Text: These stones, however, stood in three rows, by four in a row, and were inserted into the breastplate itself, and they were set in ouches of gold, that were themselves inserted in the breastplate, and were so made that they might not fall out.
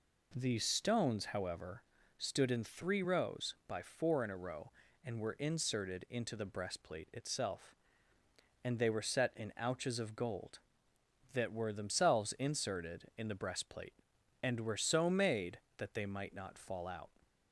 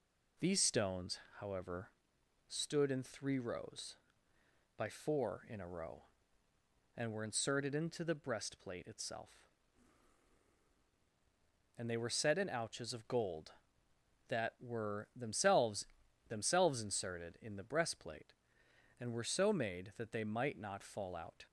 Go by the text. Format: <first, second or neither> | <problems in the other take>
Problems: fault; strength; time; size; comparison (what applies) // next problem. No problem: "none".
first | says "themselves" twice; at 16.2 s